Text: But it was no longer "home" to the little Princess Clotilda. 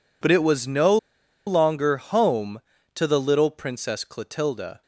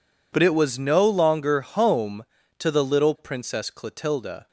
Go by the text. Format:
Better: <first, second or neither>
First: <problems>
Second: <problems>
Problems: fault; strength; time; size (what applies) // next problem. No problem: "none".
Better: second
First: pauses between "no" and "longer"; noticeable; at 0.9 s; 0.50 s long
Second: none